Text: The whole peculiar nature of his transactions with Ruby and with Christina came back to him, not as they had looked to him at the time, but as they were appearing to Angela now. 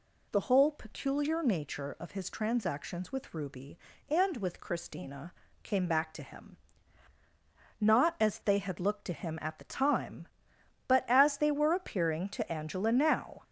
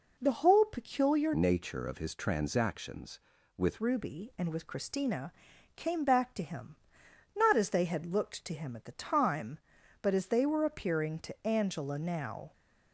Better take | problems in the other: first | changes voice from "nature" to "with"; from 1.3 to 3.7 s; 2.4 s long // pauses between "Christina" and "came"; at 5.3 s; 0.44 s long; slight in the first

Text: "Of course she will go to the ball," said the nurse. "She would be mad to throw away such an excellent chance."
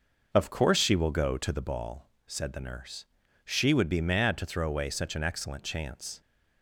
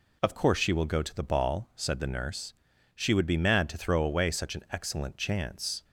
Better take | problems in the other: second | starts louder than the rest; noticeable; until 1.7 s; 6 dB

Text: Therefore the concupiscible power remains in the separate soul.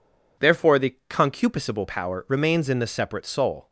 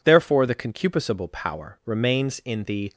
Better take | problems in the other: first | stops before "separate soul"; at 2.9 s

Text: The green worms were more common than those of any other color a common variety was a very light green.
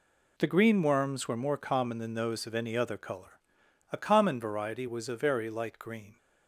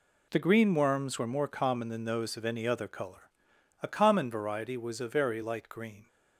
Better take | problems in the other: neither | pauses between "color" and "a"; noticeable; the same in both

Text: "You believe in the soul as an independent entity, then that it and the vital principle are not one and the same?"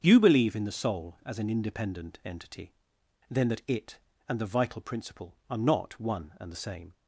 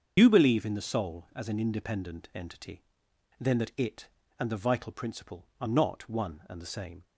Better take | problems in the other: first | loses the start of "You"; at 0.1 s; 45 ms // starts louder than the rest; until 1.1 s; 7 dB; strong in the first

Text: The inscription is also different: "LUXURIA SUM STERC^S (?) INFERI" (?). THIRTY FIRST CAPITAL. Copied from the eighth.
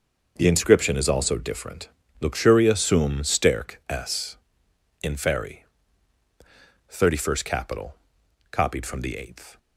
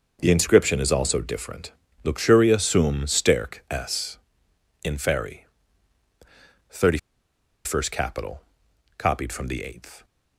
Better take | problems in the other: first | starts louder than the rest; strong; until 1.2 s; 7 dB; strong in the first // pauses between "THIRTY" and "FIRST"; noticeable; at 6.9 s; 0.68 s long

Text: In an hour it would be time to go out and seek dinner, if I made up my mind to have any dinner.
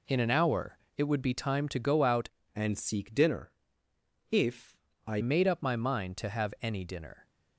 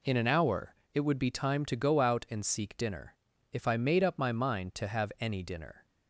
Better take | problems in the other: second | pauses between "hour" and "it"; slight; at 0.7 s; 0.20 s long; slight in the second // changes voice from "and" to "I"; from 2.5 to 5.2 s; 2.7 s long // pauses between "if" and "I"; slight; at 4.7 s; 0.28 s long

